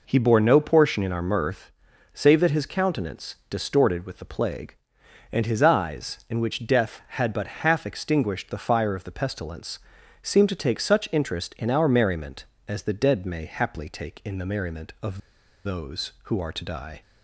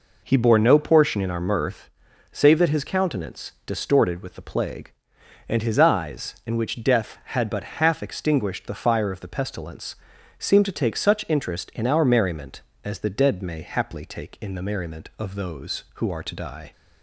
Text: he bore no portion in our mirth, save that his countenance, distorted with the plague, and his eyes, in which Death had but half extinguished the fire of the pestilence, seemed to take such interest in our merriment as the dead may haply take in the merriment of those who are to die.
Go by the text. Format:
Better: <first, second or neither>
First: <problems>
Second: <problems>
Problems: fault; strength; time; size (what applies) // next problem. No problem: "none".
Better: second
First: pauses between "of" and "those"; noticeable; at 15.1 s; 0.47 s long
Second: none